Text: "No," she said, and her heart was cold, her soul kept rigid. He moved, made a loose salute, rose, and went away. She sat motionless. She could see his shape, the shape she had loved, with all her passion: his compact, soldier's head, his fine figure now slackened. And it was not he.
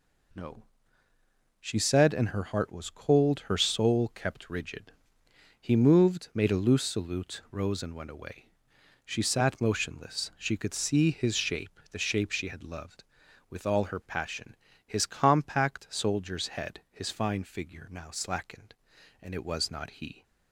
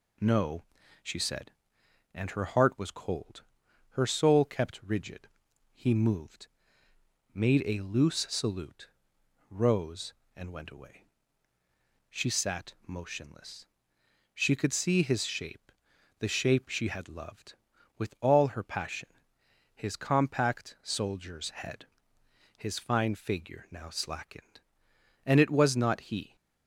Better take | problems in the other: neither | none

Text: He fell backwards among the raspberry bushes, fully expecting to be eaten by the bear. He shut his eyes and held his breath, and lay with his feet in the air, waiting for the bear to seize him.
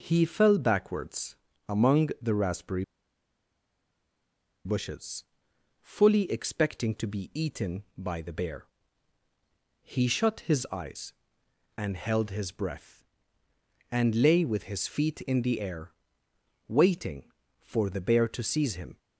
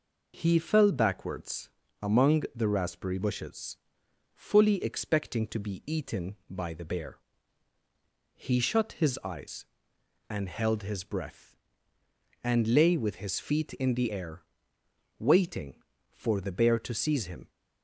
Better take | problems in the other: second | pauses between "backwards" and "among"; slight; at 1.3 s; 0.34 s long; slight in the second // pauses between "raspberry" and "bushes"; strong; at 2.8 s; 1.8 s long

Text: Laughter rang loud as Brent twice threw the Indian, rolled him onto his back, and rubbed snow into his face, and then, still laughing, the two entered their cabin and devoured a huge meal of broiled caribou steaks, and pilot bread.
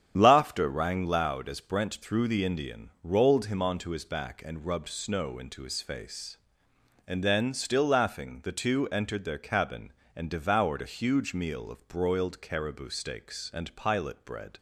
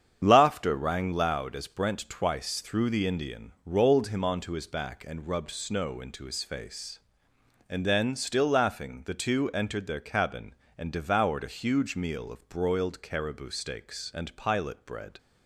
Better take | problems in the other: second | starts louder than the rest; strong; until 1.1 s; 9 dB; strong in the second // skips "twice"; at 2.0 s

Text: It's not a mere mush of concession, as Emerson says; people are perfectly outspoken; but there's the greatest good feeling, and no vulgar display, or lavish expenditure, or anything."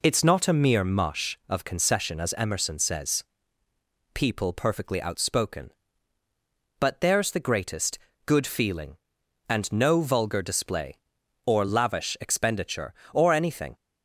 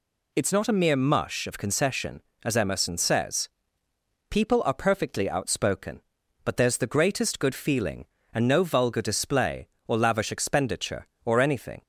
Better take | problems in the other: second | skips "are"; at 4.5 s // pauses between "greatest" and "good"; slight; at 7.9 s; 0.26 s long

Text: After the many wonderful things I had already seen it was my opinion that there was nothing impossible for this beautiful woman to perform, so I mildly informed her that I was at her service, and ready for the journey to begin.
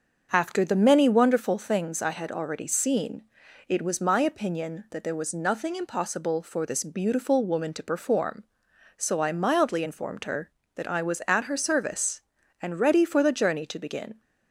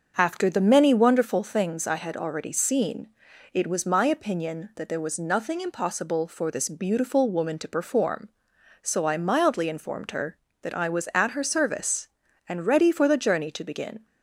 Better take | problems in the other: neither | starts louder than the rest; the same in both // pauses between "seen" and "it"; the same in both

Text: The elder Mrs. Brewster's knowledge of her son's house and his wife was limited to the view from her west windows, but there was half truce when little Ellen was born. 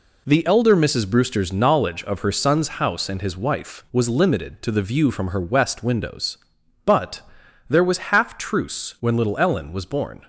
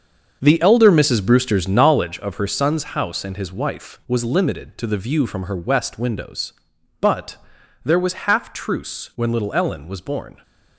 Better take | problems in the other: first | starts louder than the rest; until 2.3 s; 7 dB // pauses between "but" and "there"; noticeable; at 7.3 s; 0.48 s long; noticeable in the first

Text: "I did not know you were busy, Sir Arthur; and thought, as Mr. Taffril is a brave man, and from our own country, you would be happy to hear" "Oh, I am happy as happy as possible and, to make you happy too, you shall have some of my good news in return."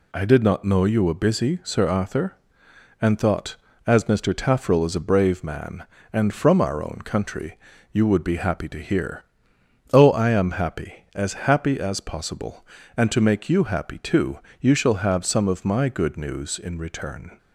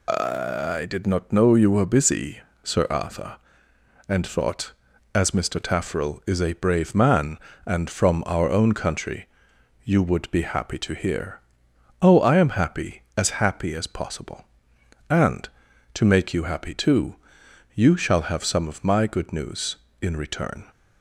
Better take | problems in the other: neither | pauses between "hear" and "Oh"; noticeable; the same in both

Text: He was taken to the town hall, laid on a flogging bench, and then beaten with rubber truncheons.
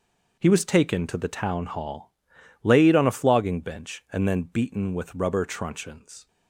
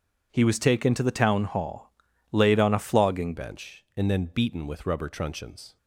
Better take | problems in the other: first | changes voice at "bench"; from 3.3 s on; 2.4 s long

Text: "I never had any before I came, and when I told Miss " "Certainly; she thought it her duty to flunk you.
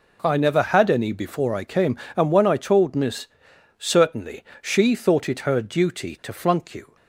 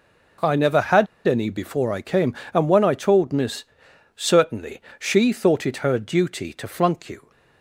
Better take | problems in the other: first | pauses between "had" and "any"; slight; at 1.0 s; 0.21 s long

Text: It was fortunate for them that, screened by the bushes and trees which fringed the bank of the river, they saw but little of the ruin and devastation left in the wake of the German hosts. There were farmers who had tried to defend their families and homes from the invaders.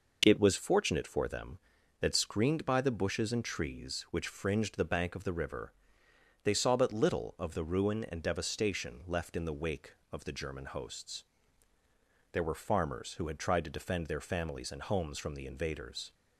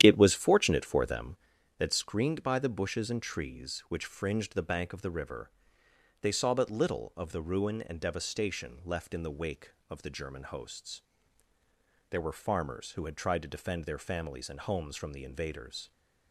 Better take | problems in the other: first | starts louder than the rest; strong; until 1.5 s; 10 dB

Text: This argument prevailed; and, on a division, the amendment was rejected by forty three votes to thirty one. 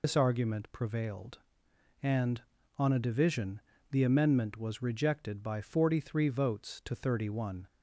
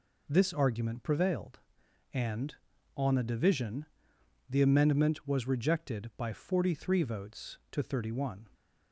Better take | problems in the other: second | loses the start of "This"; at 0.0 s; 95 ms

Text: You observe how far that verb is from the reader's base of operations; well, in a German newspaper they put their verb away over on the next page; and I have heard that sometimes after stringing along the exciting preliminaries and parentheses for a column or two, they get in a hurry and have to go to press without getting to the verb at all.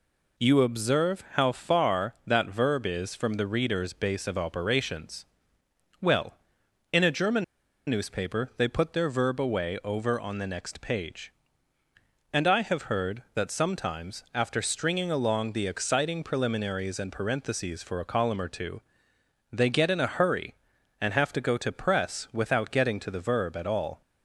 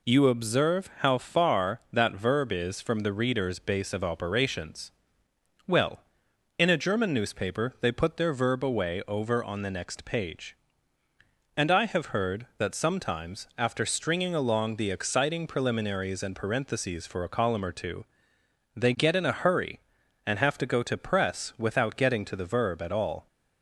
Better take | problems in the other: second | pauses between "German" and "newspaper"; at 7.4 s; 0.44 s long

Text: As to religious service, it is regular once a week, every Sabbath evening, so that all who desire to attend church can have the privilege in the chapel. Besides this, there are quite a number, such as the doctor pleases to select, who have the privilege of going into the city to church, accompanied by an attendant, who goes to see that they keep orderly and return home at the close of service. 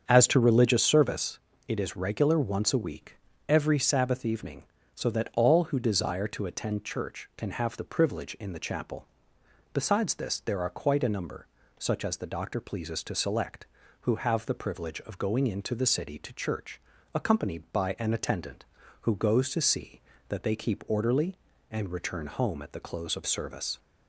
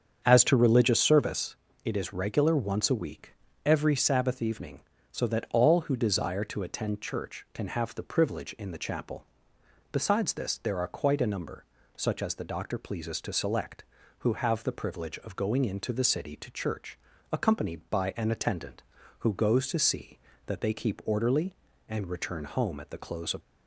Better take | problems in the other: first | starts louder than the rest; strong; until 1.2 s; 7.5 dB; strong in the first // stops before "service"; at 23.4 s

